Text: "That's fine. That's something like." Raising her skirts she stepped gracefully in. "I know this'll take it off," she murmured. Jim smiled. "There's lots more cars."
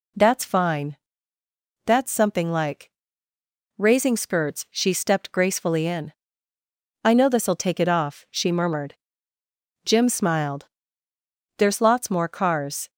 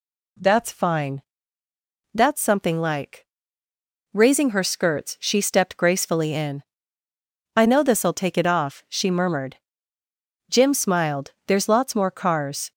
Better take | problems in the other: second | skips "her"; at 4.1 s

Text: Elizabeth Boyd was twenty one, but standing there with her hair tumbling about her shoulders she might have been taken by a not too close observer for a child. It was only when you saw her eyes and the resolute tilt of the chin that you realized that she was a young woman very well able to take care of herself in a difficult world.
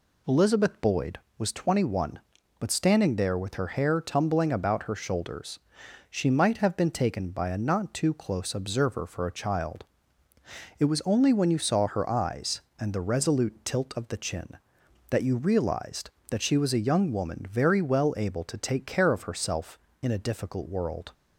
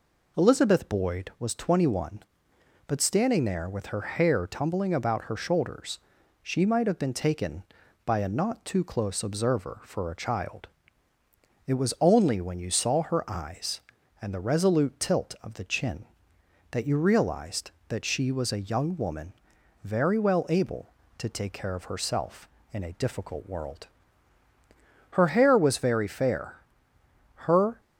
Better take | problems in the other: first | pauses between "shoulders" and "she"; at 5.9 s; 0.44 s long; noticeable in the first // pauses between "woman" and "very"; noticeable; at 19.3 s; 0.50 s long // goes on to say "Her hair was very fair her"; strong; from 25.1 s on; 2.6 s long

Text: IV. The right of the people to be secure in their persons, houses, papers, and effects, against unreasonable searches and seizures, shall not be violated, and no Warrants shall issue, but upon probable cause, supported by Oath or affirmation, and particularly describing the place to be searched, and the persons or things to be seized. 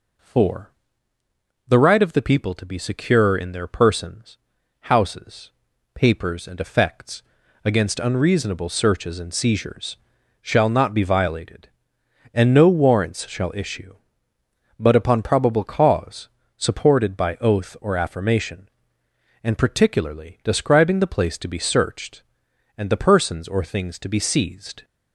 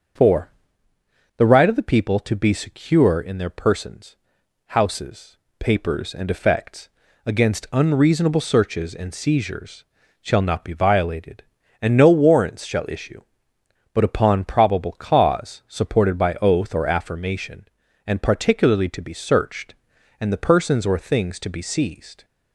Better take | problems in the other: first | starts louder than the rest; until 2.0 s; 6.5 dB // skips "describing the place"; at 18.8 s

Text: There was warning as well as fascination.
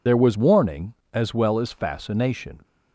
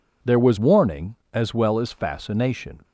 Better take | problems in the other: second | loses the start of "There"; at 0.0 s; 55 ms

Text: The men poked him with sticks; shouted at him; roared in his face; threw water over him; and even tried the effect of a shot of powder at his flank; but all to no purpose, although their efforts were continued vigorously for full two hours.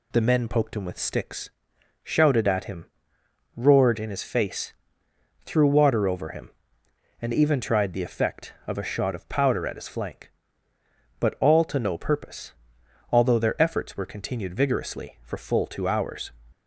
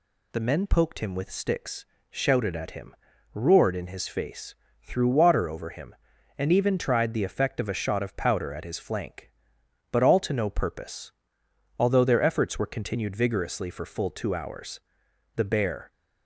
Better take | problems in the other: first | goes on to say "The bear"; from 15.3 s on; 0.56 s long

